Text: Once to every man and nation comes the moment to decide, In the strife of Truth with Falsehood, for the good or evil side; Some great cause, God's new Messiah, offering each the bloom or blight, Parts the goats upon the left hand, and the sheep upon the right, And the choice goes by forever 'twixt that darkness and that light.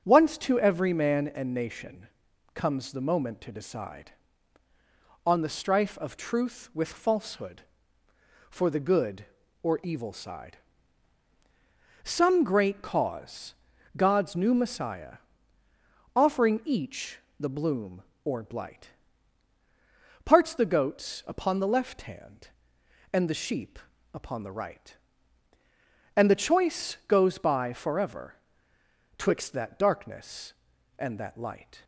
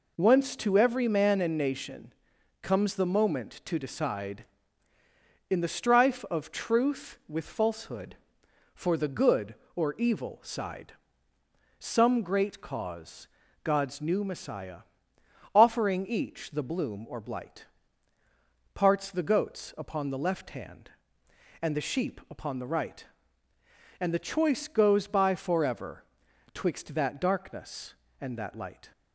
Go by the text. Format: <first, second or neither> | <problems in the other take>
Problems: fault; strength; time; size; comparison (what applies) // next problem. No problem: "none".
second | starts louder than the rest; until 1.0 s; 6.5 dB // pauses between "nation" and "comes"; noticeable; at 2.0 s; 0.48 s long; noticeable in the second // says "On" for "In"; at 5.2 s // pauses between "each" and "the"; slight; at 17.1 s; 0.20 s long // pauses between "sheep" and "upon"; at 23.7 s; 0.38 s long // pauses between "forever" and "twixt"; noticeable; at 28.3 s; 0.84 s long; noticeable in the second